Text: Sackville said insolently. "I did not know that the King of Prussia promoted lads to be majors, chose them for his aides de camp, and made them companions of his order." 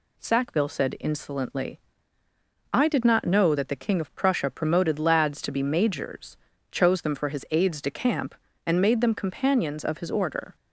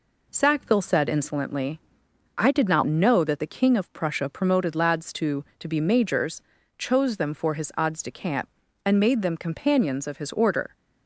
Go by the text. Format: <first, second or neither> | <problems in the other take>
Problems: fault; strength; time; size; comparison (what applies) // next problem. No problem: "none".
first | says "to" twice; at 5.5 s